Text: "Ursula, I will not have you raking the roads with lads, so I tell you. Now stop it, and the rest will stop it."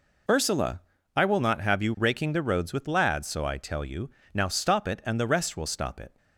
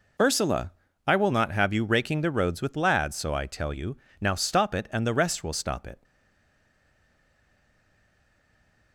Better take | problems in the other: first | stays silent after the last word; strong; from 6.0 s on; 2.9 s long

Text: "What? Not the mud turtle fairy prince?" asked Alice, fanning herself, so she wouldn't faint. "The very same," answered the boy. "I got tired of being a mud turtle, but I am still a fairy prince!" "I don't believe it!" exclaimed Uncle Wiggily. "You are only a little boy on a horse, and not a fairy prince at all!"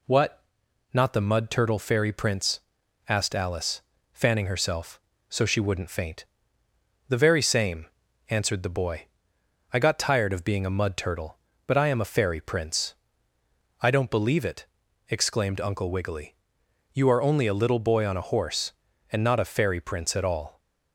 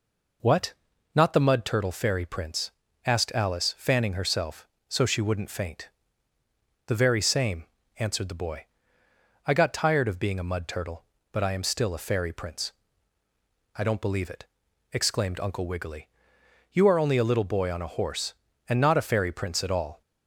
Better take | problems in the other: second | skips "still"; at 12.0 s

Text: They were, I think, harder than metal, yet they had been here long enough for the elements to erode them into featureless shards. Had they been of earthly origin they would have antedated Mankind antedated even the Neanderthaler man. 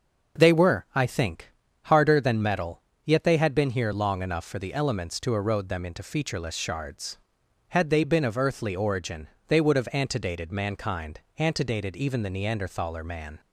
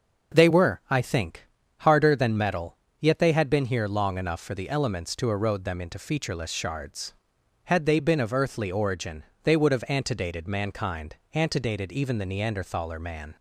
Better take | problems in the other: neither | starts louder than the rest; noticeable; the same in both // pauses between "origin" and "they"; slight; the same in both // pauses between "Mankind" and "antedated"; slight; the same in both

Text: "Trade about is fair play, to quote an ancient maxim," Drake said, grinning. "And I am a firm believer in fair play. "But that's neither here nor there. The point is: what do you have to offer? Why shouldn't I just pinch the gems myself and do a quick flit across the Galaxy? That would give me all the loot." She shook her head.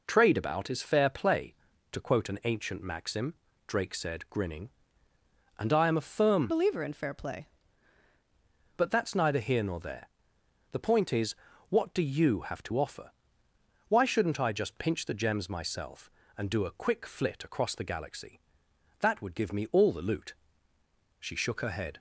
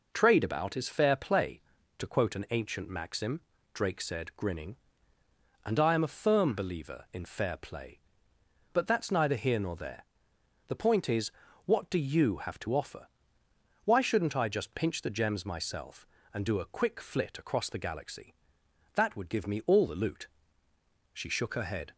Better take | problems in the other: second | changes voice from "believer" to "play"; from 6.4 to 7.4 s; 1.0 s long

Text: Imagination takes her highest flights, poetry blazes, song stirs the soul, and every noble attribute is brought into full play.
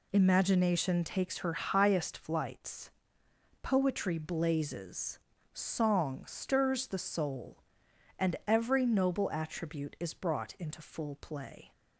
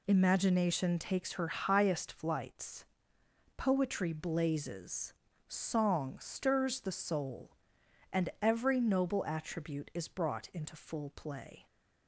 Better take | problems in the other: neither | none

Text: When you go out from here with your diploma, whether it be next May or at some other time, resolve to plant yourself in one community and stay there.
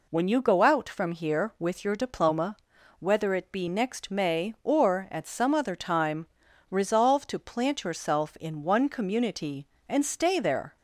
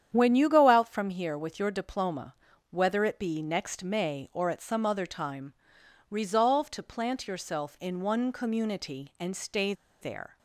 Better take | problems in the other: first | starts louder than the rest; strong; until 1.1 s; 9 dB // pauses between "stay" and "there"; slight; at 9.7 s; 0.28 s long

